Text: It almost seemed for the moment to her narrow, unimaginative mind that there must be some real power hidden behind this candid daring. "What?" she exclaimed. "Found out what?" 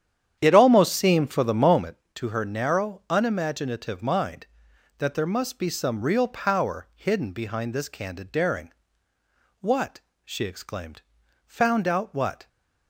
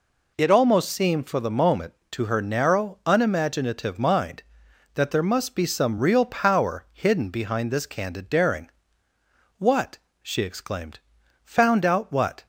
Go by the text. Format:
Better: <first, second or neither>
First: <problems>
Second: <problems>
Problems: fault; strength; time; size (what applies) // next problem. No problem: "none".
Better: second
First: starts louder than the rest; strong; until 1.9 s; 9.5 dB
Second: none